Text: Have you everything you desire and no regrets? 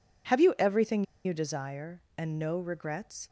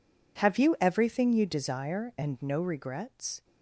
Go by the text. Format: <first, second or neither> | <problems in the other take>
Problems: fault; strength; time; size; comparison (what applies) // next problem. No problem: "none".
second | pauses between "everything" and "you"; slight; at 1.0 s; 0.20 s long